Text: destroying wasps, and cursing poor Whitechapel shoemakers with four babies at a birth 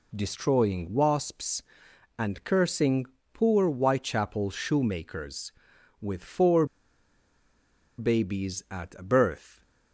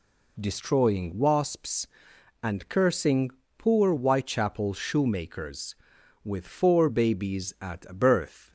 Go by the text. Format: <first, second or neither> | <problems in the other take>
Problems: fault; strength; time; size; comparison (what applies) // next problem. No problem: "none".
second | pauses between "cursing" and "poor"; slight; at 3.0 s; 0.28 s long; slight in the second // pauses between "four" and "babies"; strong; at 6.6 s; 1.3 s long